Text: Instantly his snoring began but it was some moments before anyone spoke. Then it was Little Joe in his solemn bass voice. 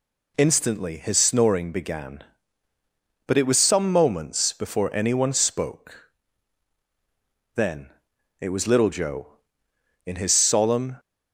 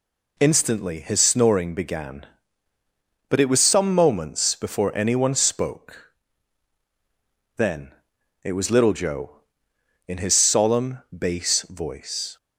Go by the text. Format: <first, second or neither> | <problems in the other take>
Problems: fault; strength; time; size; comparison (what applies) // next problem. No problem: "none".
second | pauses between "Then" and "it"; noticeable; at 7.8 s; 0.52 s long; noticeable in the second // stops before "bass voice"; at 10.9 s